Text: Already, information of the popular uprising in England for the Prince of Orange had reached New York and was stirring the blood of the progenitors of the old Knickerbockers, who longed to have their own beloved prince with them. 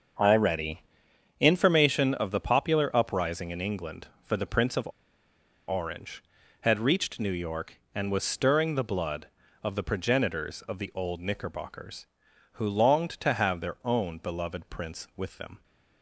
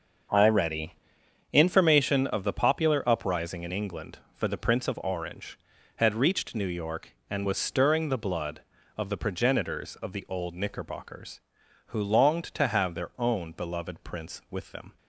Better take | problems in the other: second | starts louder than the rest; until 1.7 s; 6.5 dB; also in the second // pauses between "of" and "Orange"; noticeable; at 4.8 s; 0.78 s long

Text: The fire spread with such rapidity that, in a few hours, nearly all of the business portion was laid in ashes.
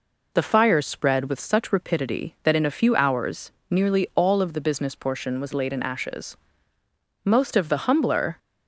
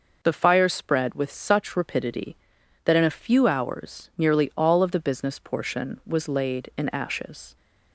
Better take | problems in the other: second | goes on to say "Most of the humbler"; noticeable; from 7.2 s on; 1.1 s long

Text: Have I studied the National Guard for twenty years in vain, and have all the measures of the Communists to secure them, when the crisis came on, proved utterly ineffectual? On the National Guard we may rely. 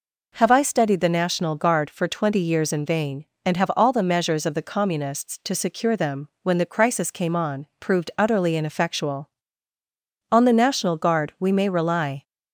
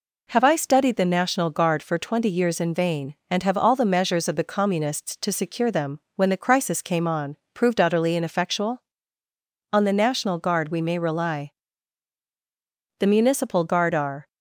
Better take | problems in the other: first | goes on to say "The Municipal Guard are"; noticeable; from 12.9 s on; 1.2 s long

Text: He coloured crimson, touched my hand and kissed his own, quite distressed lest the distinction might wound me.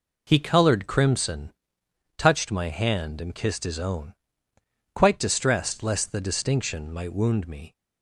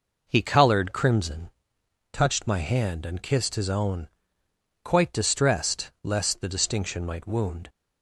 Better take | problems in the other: first | stops before "me"; at 7.6 s

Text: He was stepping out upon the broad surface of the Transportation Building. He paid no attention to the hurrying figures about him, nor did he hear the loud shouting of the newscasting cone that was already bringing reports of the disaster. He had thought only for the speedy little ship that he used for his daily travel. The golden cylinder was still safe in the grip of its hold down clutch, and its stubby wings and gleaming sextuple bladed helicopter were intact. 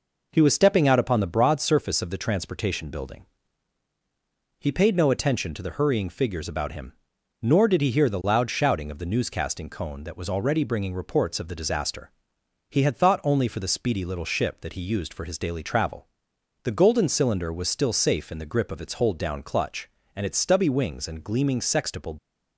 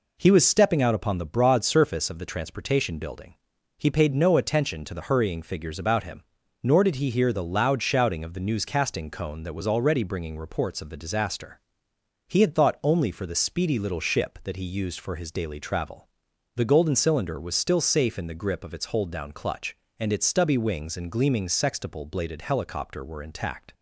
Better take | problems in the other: second | stops before "bladed helicopter were intact"; at 22.1 s

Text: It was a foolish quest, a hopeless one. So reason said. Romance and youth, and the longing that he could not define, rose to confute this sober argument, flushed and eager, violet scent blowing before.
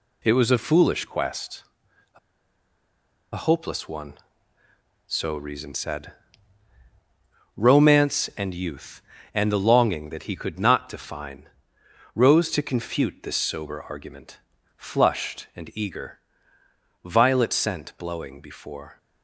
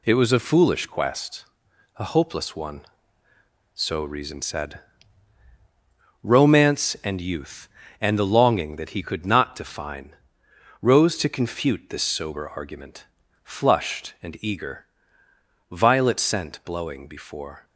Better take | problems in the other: second | pauses between "a" and "hopeless"; at 2.1 s; 1.1 s long

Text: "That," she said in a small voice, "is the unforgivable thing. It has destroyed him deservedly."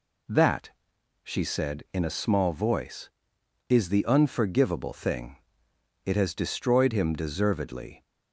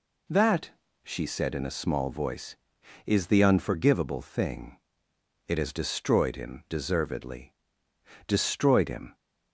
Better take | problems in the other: first | goes on to say "Destroyed him"; noticeable; from 8.2 s on; 0.88 s long

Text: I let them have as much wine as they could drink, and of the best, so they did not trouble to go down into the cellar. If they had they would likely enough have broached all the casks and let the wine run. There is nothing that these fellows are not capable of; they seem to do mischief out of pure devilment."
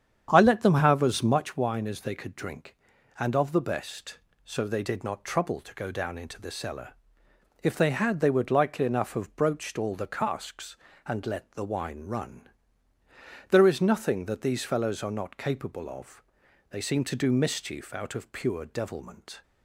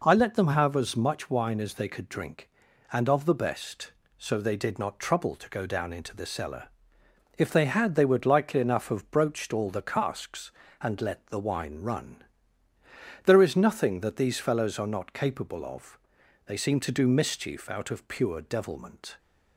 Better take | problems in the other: second | starts louder than the rest; strong; until 1.7 s; 8.5 dB

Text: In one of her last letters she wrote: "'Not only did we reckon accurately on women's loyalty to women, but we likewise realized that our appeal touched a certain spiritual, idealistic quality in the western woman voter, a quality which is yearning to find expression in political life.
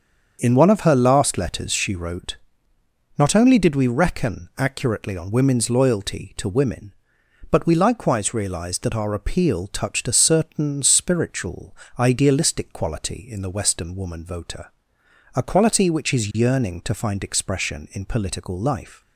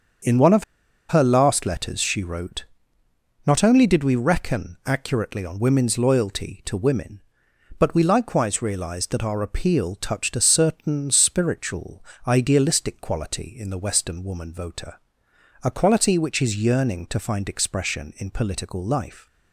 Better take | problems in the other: first | starts louder than the rest; until 1.7 s; 7 dB; also in the first // pauses between "of" and "her"; noticeable; at 0.6 s; 0.46 s long

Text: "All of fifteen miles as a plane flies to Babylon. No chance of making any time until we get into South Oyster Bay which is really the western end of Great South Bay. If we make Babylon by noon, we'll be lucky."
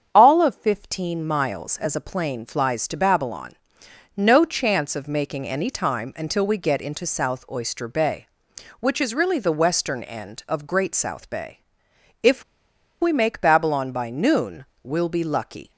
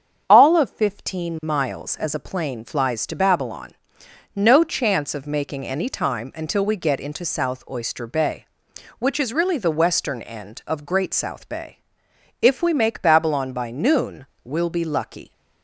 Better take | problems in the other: second | starts louder than the rest; strong; until 1.1 s; 7.5 dB; strong in the second // pauses between "If" and "we"; noticeable; at 12.4 s; 0.58 s long

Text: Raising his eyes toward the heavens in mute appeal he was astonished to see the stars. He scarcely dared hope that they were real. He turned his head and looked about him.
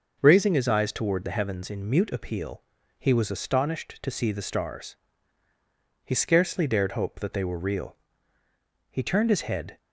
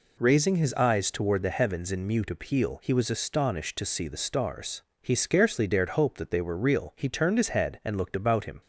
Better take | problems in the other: second | pauses between "appeal" and "he"; slight; at 2.6 s; 0.34 s long // stops before "and looked about him"; at 9.7 s

